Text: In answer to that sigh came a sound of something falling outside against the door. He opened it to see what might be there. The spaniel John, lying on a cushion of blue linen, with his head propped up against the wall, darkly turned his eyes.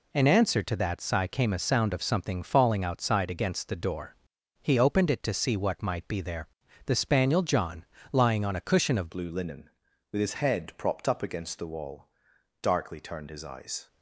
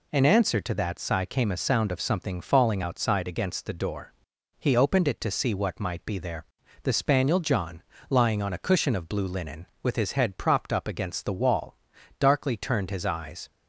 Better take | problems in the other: second | changes voice at "blue"; from 9.0 s on; 4.8 s long

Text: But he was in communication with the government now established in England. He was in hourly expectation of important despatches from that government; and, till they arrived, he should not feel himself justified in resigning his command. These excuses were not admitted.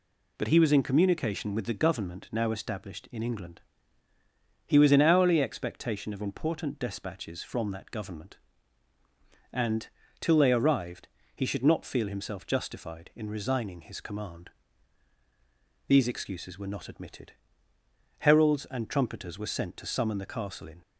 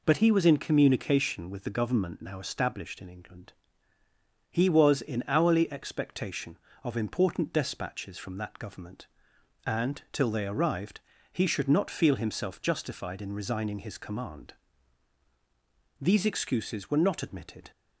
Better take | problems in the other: second | goes on to say "Heralds and trumpeters were sent to summon the Castle in"; strong; from 18.1 s on; 2.6 s long

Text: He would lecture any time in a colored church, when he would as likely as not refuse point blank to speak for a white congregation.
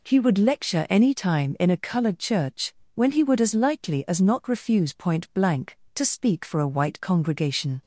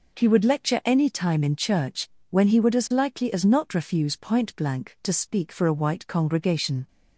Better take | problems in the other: first | skips "a colored"; at 1.5 s

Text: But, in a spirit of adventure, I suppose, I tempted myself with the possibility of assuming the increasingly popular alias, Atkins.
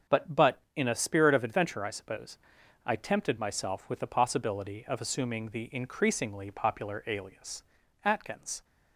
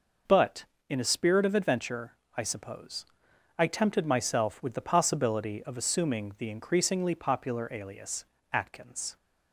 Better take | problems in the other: second | starts louder than the rest; until 1.2 s; 6.5 dB // says "But" twice; at 0.3 s

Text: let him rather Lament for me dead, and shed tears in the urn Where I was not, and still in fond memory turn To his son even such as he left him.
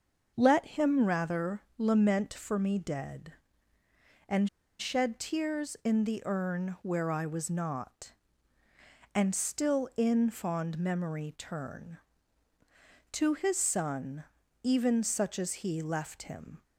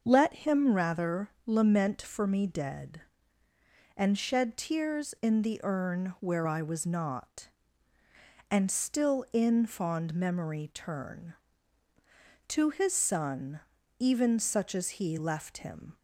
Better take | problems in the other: second | starts louder than the rest; until 1.3 s; 6 dB; also in the second // pauses between "rather" and "Lament"; slight; at 1.6 s; 0.16 s long; slight in the second // pauses between "and" and "shed"; slight; at 4.4 s; 0.31 s long // pauses between "son" and "even"; at 14.2 s; 0.40 s long; also in the second

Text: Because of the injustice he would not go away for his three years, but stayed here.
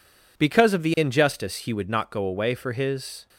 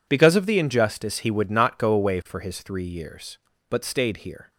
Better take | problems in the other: second | stops before "three years but stayed here"; at 3.2 s

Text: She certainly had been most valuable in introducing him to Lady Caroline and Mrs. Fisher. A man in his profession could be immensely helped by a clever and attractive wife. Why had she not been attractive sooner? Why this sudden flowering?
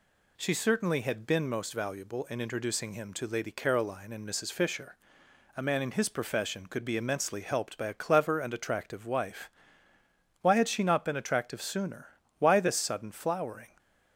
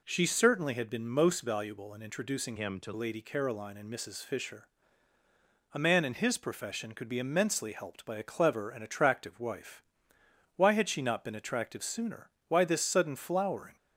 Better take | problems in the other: first | changes voice from "him" to "to"; from 2.5 to 2.9 s; 0.4 s long

